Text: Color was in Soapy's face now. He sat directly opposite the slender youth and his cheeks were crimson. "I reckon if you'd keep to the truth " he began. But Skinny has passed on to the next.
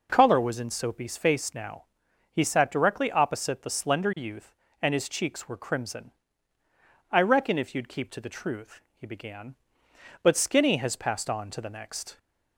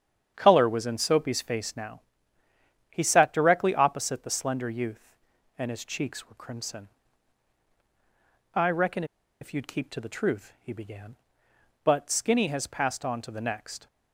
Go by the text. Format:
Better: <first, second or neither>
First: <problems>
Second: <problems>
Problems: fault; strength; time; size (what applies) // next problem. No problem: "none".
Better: first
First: none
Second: starts louder than the rest; strong; until 1.3 s; 8.5 dB // pauses between "reckon" and "if"; at 9.0 s; 0.36 s long